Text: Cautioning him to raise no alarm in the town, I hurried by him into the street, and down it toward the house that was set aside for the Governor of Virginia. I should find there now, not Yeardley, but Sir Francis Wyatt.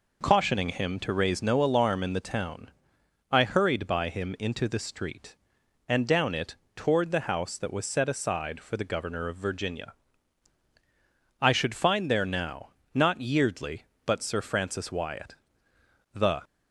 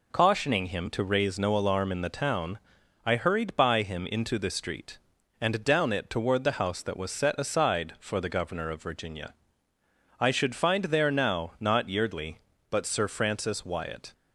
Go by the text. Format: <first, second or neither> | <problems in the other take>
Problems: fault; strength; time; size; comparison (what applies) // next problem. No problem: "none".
second | pauses between "it" and "toward"; slight; at 6.5 s; 0.22 s long // goes on to say "The"; slight; from 16.1 s on; 0.28 s long